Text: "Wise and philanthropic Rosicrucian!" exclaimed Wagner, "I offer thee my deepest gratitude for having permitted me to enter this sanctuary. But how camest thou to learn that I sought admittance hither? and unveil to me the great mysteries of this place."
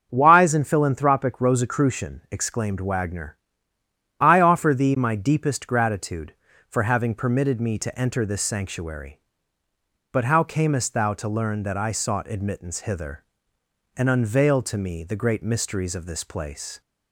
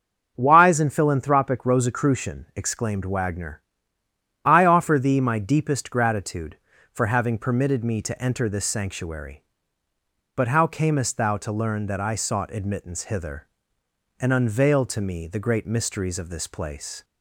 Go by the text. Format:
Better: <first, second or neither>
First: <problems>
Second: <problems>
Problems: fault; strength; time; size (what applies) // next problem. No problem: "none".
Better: neither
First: starts louder than the rest; until 1.1 s; 7 dB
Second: starts louder than the rest; until 1.3 s; 7 dB